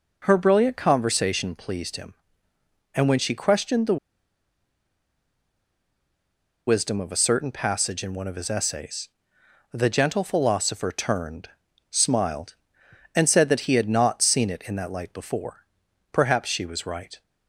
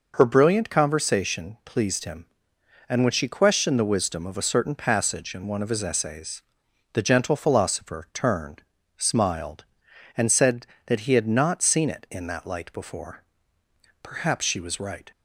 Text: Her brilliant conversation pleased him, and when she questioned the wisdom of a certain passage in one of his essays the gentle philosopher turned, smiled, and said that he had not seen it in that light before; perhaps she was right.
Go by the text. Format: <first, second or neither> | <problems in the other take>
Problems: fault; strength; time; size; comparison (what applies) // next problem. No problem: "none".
second | pauses between "the" and "wisdom"; strong; at 3.9 s; 2.7 s long // pauses between "essays" and "the"; noticeable; at 9.0 s; 0.64 s long; noticeable in the second